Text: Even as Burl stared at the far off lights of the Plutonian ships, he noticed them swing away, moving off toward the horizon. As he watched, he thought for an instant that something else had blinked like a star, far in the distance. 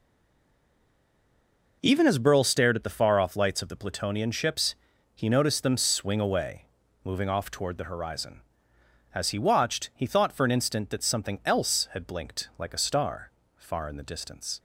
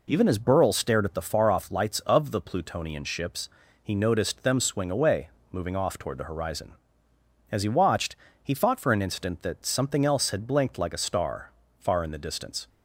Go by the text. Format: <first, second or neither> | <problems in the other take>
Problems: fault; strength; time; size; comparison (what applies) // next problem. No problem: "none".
second | stays silent before the first word; noticeable; until 1.8 s; 1.8 s long